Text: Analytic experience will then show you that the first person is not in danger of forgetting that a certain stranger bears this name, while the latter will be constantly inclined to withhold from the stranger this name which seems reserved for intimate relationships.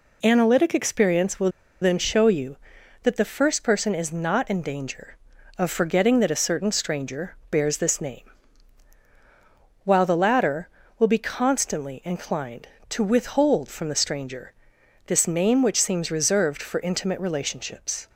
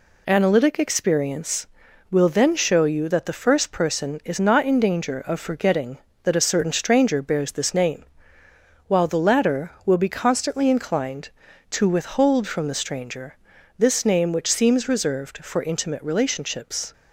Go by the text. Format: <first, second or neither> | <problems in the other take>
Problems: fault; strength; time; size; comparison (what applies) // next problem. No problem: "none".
second | pauses between "will" and "then"; slight; at 1.4 s; 0.33 s long // pauses between "stranger" and "this"; noticeable; at 14.5 s; 0.56 s long; also in the second